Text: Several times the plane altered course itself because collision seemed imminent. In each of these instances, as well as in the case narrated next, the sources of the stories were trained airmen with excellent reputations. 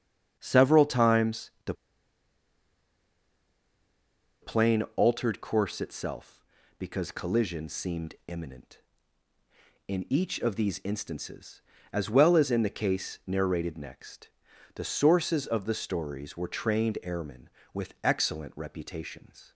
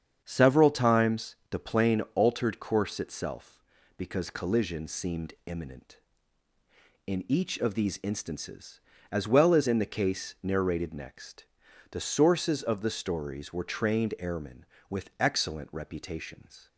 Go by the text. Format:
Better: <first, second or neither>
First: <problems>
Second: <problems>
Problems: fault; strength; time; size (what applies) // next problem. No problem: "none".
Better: second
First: starts louder than the rest; strong; until 1.4 s; 8 dB // pauses between "the" and "plane"; strong; at 1.7 s; 2.6 s long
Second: starts louder than the rest; strong; until 1.2 s; 7.5 dB